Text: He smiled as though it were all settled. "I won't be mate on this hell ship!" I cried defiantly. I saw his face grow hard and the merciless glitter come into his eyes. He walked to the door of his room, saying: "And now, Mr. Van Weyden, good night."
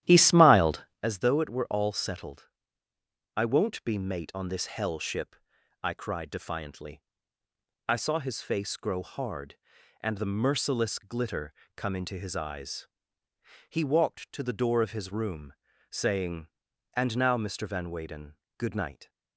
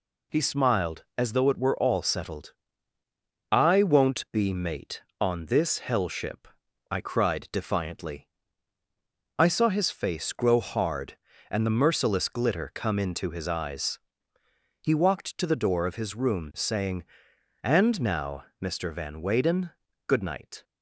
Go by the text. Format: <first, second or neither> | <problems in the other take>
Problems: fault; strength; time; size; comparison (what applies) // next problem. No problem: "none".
second | starts louder than the rest; strong; until 1.1 s; 12 dB // pauses between "glitter" and "come"; slight; at 11.5 s; 0.22 s long